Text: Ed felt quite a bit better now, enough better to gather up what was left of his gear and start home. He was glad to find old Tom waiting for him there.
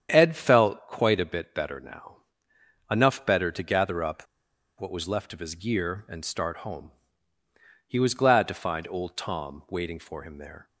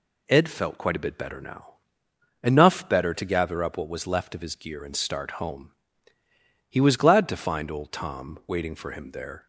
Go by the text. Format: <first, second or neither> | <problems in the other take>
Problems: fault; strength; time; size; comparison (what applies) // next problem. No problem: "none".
second | starts louder than the rest; strong; until 1.1 s; 8.5 dB // pauses between "up" and "what"; noticeable; at 4.2 s; 0.53 s long